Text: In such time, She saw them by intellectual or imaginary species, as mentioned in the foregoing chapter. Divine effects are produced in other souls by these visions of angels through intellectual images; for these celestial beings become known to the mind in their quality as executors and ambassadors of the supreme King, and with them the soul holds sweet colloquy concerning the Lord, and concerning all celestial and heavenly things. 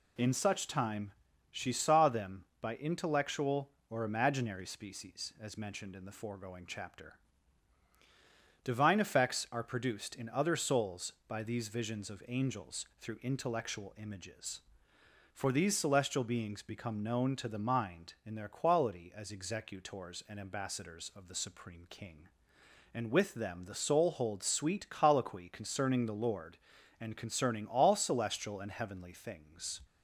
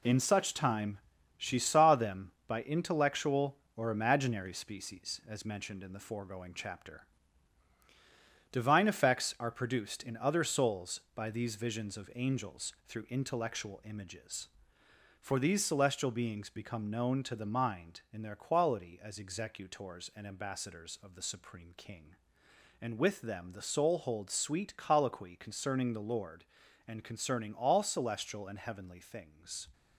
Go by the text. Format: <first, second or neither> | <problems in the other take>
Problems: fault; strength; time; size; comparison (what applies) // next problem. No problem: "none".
first | gets quieter; strong; throughout; 7.5 dB